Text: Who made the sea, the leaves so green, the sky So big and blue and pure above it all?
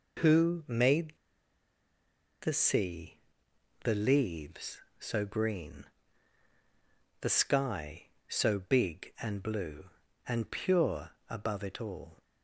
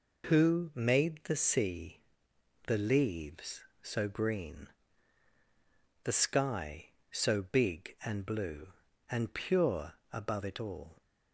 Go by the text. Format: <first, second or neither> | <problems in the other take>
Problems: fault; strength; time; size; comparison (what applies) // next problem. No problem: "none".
second | pauses between "made" and "the"; strong; at 1.1 s; 1.3 s long // pauses between "pure" and "above"; slight; at 11.1 s; 0.18 s long; slight in the second